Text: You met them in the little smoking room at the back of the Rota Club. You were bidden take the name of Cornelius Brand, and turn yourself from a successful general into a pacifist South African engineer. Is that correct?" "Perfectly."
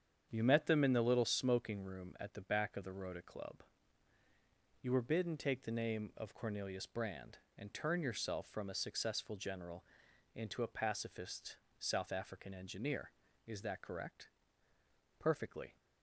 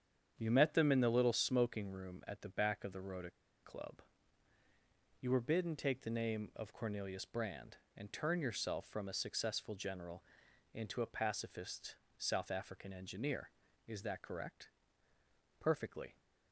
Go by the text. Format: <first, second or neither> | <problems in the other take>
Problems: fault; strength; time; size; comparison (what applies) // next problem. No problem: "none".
first | starts louder than the rest; strong; until 1.3 s; 8 dB; strong in the first // pauses between "Rota" and "Club"; slight; at 3.3 s; 0.32 s long // pauses between "general" and "into"; noticeable; at 10.2 s; 0.52 s long; noticeable in the first // pauses between "pacifist" and "South"; slight; at 11.9 s; 0.24 s long; slight in the first